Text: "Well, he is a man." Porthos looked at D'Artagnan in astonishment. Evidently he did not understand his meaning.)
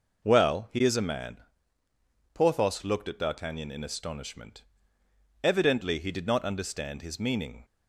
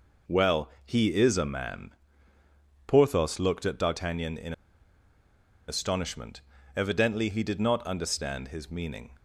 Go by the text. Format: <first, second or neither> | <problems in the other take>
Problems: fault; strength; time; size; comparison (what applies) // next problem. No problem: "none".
first | pauses between "in" and "astonishment"; at 4.5 s; 1.1 s long